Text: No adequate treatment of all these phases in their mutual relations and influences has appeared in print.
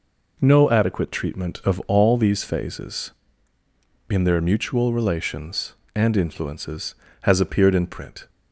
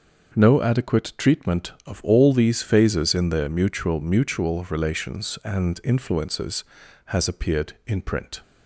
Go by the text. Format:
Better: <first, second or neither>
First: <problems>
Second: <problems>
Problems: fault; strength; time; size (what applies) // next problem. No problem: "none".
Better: first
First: none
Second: starts louder than the rest; noticeable; until 1.4 s; 6 dB // says "mutual" twice; at 3.9 s